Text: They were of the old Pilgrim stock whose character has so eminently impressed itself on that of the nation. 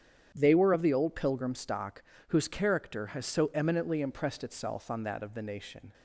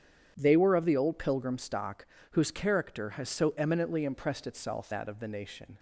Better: first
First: starts louder than the rest; strong; until 1.3 s; 8.5 dB // pauses between "stock" and "whose"; slight; at 2.0 s; 0.26 s long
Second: starts louder than the rest; strong; until 1.3 s; 8.5 dB // pauses between "stock" and "whose"; slight; at 2.0 s; 0.26 s long // skips "on"; at 4.9 s

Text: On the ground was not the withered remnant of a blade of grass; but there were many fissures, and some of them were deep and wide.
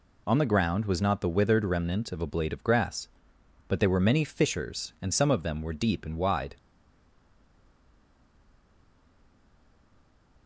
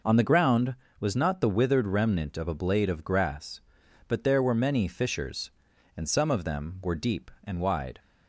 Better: second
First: stays silent after the last word; strong; from 6.5 s on; 3.9 s long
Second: none

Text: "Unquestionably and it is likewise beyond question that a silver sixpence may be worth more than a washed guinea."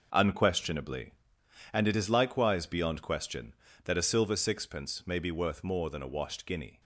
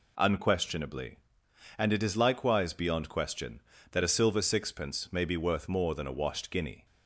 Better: second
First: gets quieter; strong; throughout; 9.5 dB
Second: none

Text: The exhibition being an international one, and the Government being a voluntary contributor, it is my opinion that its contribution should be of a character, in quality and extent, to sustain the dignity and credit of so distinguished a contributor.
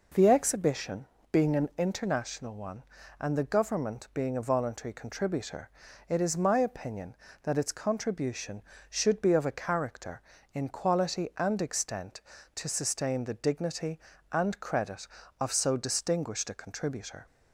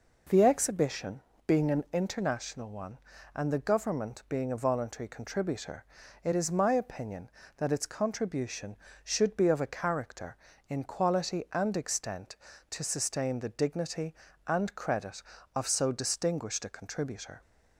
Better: neither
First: pauses between "exhibition" and "being"; slight; at 1.0 s; 0.24 s long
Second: pauses between "exhibition" and "being"; slight; at 1.2 s; 0.24 s long

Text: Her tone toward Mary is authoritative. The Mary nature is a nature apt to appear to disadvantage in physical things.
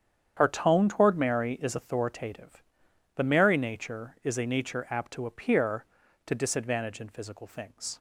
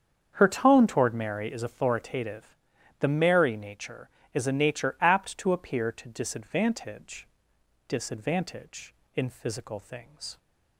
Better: first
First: starts louder than the rest; strong; until 1.3 s; 8.5 dB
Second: starts louder than the rest; strong; until 1.3 s; 7.5 dB // says "disadvantage" twice; at 7.8 s

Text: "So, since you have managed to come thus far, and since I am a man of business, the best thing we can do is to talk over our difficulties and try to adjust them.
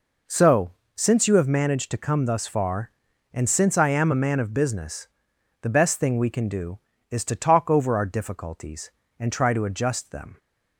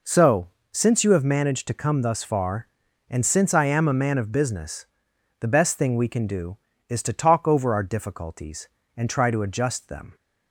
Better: neither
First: none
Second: none

